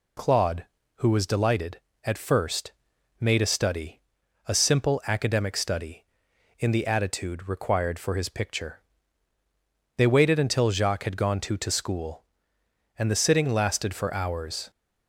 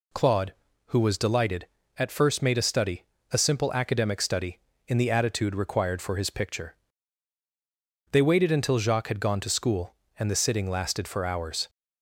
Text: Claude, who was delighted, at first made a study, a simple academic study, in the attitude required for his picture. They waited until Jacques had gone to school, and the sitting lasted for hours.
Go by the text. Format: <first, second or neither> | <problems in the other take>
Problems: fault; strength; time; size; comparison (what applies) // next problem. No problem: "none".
second | pauses between "first" and "made"; noticeable; at 2.7 s; 0.48 s long // says "to" twice; at 11.5 s